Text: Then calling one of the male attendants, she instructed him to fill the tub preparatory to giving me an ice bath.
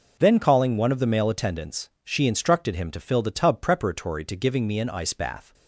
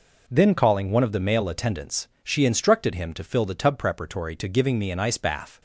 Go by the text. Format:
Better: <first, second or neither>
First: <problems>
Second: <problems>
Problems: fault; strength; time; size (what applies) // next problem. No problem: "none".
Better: neither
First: none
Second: none